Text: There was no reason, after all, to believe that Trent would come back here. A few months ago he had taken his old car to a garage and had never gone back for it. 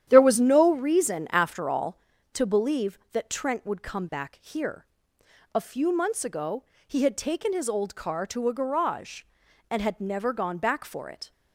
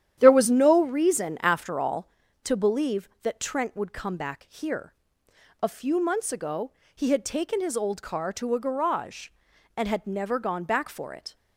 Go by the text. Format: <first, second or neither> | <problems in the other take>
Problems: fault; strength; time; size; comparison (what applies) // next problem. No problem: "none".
neither | starts louder than the rest; strong; the same in both // pauses between "ago" and "he"; slight; the same in both